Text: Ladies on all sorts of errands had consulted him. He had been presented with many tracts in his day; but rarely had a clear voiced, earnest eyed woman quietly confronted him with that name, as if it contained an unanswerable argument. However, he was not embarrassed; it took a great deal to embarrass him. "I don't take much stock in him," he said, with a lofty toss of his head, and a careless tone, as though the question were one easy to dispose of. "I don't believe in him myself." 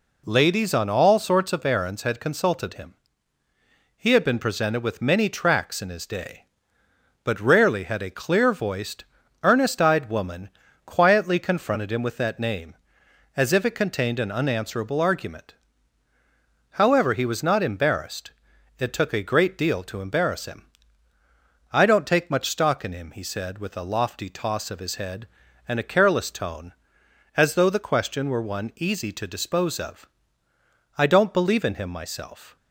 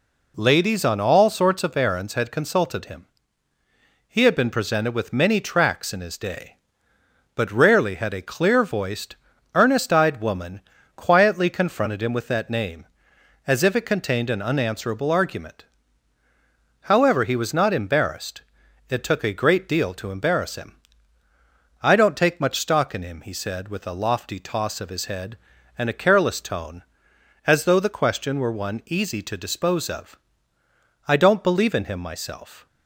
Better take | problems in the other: neither | pauses between "woman" and "quietly"; the same in both

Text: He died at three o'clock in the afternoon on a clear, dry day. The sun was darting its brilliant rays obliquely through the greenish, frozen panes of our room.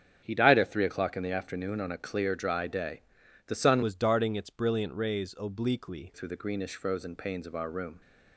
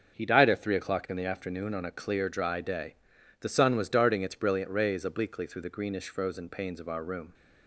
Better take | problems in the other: second | starts louder than the rest; strong; until 1.2 s; 8.5 dB; also in the second // changes voice from "was" to "obliquely"; from 3.8 to 6.1 s; 2.3 s long

